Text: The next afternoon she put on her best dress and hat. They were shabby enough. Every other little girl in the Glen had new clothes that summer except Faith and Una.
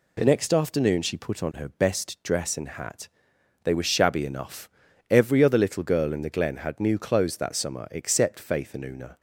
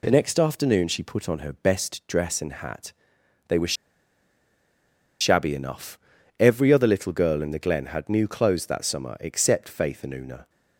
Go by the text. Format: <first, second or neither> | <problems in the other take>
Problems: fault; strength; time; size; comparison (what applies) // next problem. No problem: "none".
first | pauses between "were" and "shabby"; strong; at 3.7 s; 1.4 s long